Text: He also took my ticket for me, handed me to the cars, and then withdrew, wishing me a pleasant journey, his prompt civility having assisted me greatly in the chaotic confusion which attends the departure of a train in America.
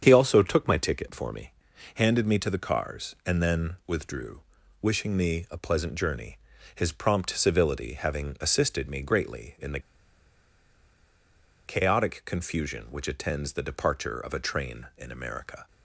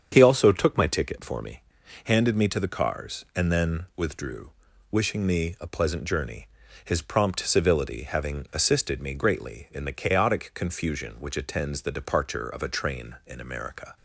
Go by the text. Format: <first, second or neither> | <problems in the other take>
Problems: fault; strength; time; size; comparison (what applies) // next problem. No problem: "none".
second | starts louder than the rest; strong; until 1.0 s; 8 dB; strong in the second // pauses between "the" and "chaotic"; strong; at 9.7 s; 1.8 s long